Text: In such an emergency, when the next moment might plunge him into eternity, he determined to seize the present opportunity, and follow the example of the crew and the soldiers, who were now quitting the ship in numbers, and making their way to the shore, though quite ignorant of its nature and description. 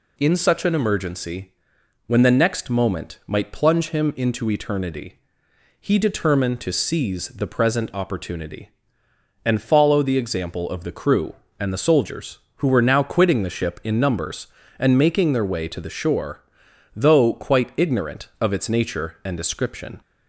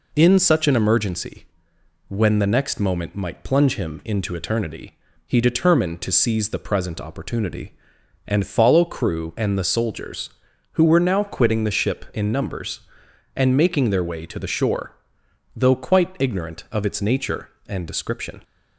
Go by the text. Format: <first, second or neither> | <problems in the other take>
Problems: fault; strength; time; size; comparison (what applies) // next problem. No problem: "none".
first | skips "the example of the"; at 8.8 s